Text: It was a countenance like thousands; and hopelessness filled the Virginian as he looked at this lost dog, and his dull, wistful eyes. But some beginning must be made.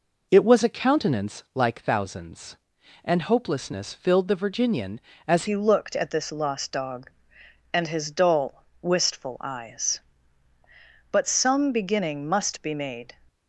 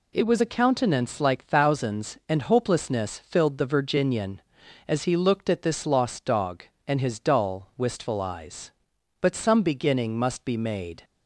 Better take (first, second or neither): second